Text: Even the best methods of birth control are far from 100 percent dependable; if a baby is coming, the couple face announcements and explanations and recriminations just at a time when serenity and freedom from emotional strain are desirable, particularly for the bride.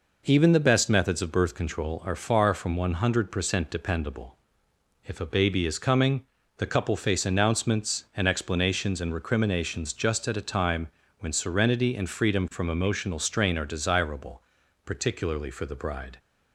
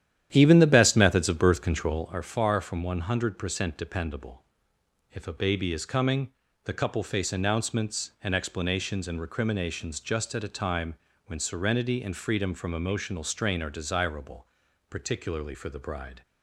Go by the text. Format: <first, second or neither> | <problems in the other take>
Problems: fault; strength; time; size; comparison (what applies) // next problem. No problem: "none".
first | starts louder than the rest; strong; until 2.2 s; 10.5 dB // pauses between "time" and "when"; slight; at 10.9 s; 0.30 s long; slight in the first